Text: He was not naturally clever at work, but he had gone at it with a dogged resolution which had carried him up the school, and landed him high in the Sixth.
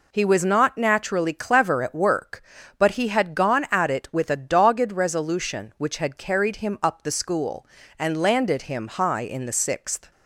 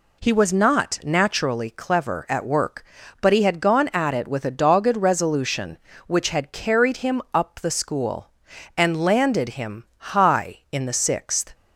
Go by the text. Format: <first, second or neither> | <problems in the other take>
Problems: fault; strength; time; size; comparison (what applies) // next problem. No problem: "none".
neither | none